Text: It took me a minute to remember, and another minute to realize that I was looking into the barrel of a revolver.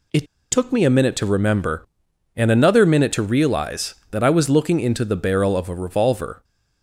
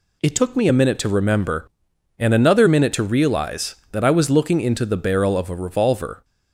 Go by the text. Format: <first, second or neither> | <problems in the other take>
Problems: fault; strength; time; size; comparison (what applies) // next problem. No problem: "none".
second | pauses between "It" and "took"; slight; at 0.2 s; 0.27 s long